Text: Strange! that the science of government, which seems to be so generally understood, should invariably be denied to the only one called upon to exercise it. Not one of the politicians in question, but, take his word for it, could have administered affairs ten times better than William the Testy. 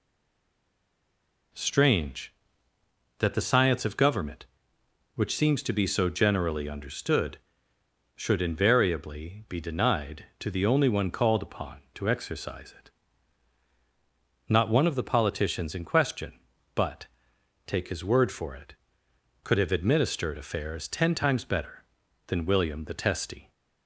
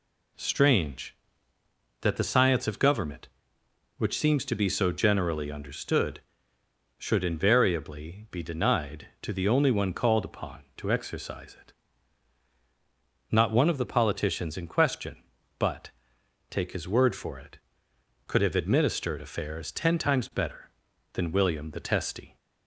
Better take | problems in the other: second | stays silent before the first word; noticeable; until 1.5 s; 1.5 s long

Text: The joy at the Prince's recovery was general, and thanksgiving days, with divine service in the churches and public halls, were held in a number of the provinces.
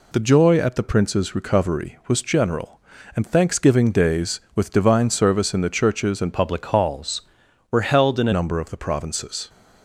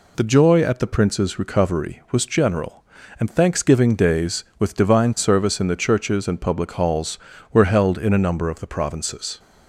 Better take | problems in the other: second | changes voice from "public" to "a"; from 6.3 to 8.3 s; 2.0 s long

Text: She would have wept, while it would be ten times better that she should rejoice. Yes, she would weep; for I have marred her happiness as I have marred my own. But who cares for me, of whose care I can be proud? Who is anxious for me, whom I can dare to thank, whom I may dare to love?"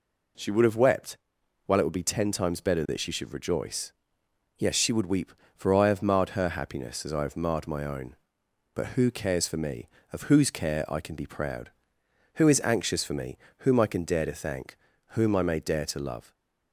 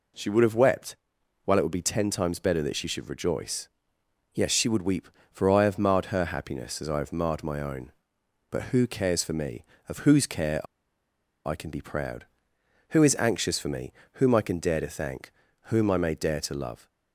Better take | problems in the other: first | pauses between "care" and "I"; noticeable; at 10.6 s; 0.79 s long

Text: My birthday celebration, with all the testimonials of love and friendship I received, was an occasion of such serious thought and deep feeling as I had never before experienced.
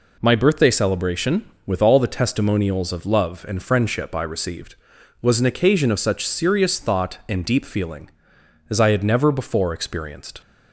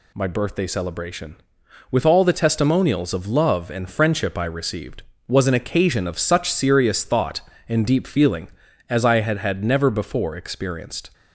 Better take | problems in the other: first | says "had" twice; at 9.3 s

